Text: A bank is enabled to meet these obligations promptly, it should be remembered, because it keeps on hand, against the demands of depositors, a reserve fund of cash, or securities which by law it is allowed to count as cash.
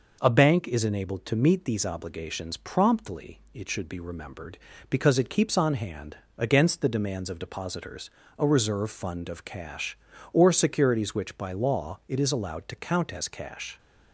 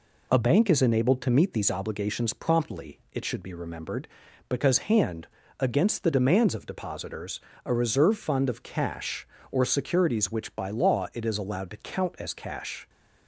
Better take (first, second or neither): first